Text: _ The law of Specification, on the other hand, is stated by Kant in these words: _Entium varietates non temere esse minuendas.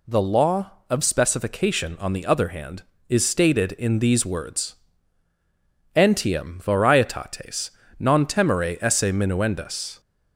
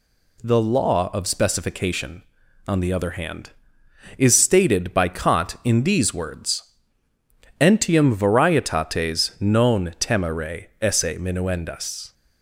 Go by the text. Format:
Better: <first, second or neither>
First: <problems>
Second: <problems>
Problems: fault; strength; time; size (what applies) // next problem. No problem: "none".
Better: second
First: skips "by Kant"; at 3.7 s // pauses between "varietates" and "non"; slight; at 7.6 s; 0.30 s long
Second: none